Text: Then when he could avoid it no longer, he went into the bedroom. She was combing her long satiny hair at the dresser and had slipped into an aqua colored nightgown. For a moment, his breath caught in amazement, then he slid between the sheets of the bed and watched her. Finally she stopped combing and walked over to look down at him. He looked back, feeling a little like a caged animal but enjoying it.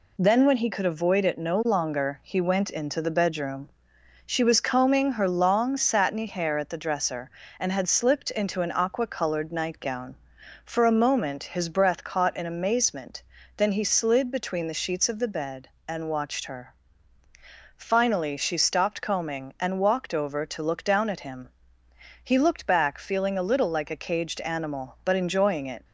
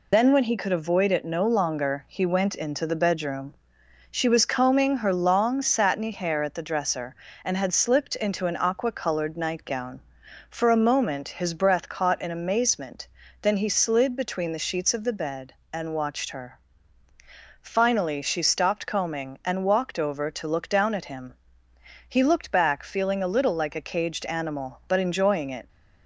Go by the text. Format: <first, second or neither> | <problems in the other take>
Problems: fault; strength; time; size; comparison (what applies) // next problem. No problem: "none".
first | loses the start of "Then"; at 0.1 s; 75 ms